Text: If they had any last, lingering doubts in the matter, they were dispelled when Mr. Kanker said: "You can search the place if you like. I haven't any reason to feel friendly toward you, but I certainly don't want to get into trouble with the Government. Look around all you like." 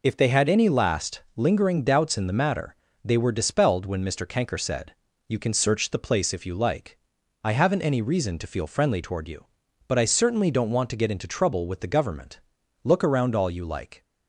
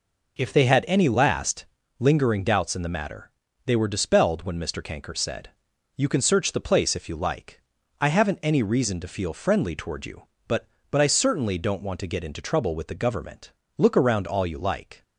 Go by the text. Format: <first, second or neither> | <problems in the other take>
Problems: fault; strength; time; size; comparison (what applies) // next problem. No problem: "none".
first | says "but" twice; at 10.9 s